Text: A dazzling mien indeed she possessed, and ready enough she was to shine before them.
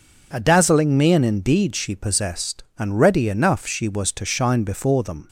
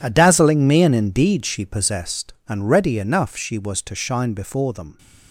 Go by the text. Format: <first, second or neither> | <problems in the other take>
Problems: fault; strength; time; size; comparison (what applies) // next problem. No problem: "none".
first | gets quieter; strong; throughout; 14 dB